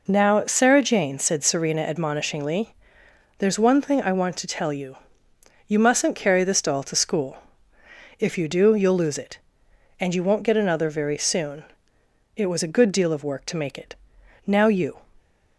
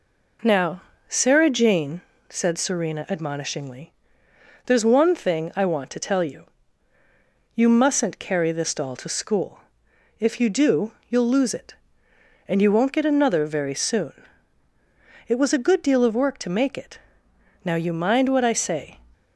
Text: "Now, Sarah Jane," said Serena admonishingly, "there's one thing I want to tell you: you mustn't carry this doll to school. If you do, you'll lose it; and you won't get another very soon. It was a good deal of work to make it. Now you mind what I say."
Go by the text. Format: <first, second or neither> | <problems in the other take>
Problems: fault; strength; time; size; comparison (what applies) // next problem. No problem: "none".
second | stops before "mind what I say"; at 15.1 s